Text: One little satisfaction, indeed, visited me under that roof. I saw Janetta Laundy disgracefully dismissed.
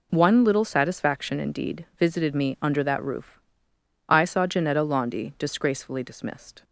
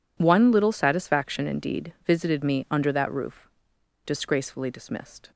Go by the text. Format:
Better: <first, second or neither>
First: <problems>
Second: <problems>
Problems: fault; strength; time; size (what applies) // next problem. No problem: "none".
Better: first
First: none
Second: skips "I saw Janetta Laundy"; at 3.7 s